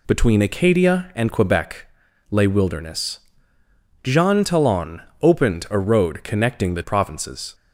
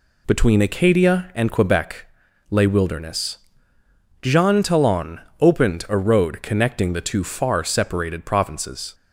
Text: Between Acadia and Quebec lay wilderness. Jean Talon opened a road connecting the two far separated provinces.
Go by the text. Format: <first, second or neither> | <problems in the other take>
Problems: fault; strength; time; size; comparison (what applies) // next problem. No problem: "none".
second | pauses between "Quebec" and "lay"; at 1.8 s; 0.42 s long; also in the second // pauses between "Talon" and "opened"; slight; at 5.0 s; 0.18 s long; slight in the second // skips "two far separated"; at 6.8 s